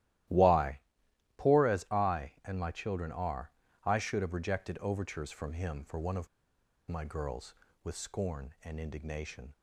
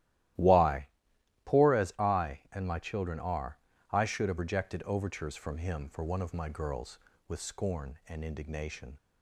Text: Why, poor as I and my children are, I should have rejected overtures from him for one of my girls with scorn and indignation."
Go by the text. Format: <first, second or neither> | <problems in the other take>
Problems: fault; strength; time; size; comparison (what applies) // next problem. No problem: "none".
second | starts louder than the rest; strong; until 1.9 s; 14.5 dB; strong in the second // pauses between "of" and "my"; noticeable; at 6.2 s; 0.60 s long